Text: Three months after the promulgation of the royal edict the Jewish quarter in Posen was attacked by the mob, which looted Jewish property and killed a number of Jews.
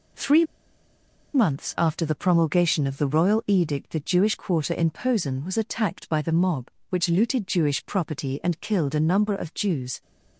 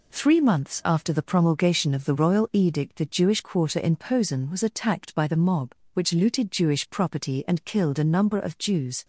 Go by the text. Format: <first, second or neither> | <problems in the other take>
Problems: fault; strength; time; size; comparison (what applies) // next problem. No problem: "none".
second | pauses between "Three" and "months"; noticeable; at 0.4 s; 0.89 s long